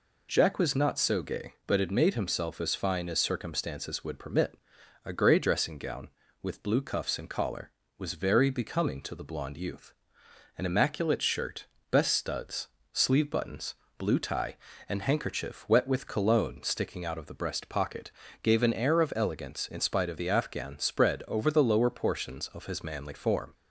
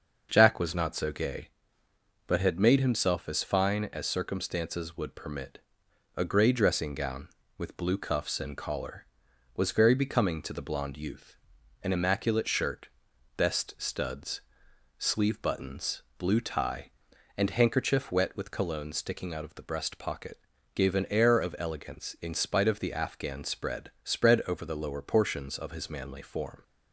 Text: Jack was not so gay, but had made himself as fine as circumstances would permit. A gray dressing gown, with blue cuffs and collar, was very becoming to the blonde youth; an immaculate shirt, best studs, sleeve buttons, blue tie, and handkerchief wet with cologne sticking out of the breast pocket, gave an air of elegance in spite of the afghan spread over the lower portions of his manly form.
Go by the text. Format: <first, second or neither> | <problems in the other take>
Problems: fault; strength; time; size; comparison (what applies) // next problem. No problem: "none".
first | starts louder than the rest; until 1.3 s; 6.5 dB // says "spread" twice; at 24.0 s